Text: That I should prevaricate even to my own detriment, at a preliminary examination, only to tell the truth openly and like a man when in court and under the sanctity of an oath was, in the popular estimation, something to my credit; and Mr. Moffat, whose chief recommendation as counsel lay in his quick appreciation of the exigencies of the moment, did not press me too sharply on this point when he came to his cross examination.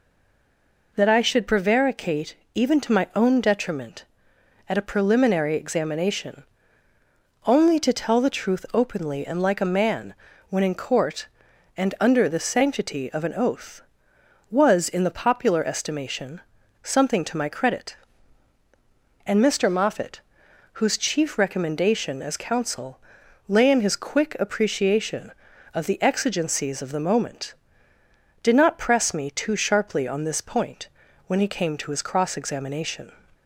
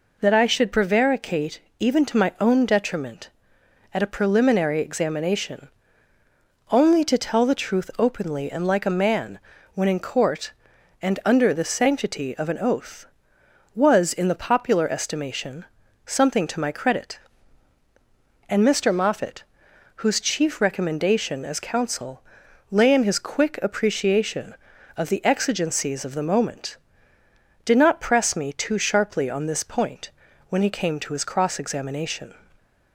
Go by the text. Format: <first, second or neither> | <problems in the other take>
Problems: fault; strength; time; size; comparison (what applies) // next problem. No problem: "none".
second | stays silent before the first word; slight; until 0.9 s; 0.9 s long // pauses between "prevaricate" and "even"; slight; at 2.3 s; 0.18 s long; slight in the second // pauses between "man" and "when"; at 10.1 s; 0.38 s long; also in the second // pauses between "counsel" and "lay"; noticeable; at 22.9 s; 0.48 s long; noticeable in the second // pauses between "point" and "when"; at 30.8 s; 0.40 s long; also in the second